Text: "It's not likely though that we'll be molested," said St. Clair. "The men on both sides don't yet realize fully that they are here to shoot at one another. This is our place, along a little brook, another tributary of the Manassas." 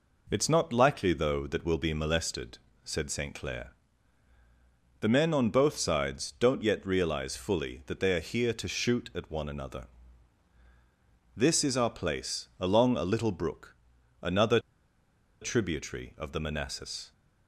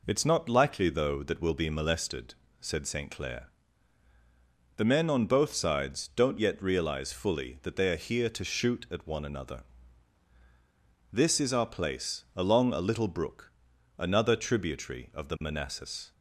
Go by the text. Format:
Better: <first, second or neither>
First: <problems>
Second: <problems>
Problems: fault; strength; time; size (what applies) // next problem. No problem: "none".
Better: second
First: pauses between "another" and "tributary"; noticeable; at 14.5 s; 0.81 s long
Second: none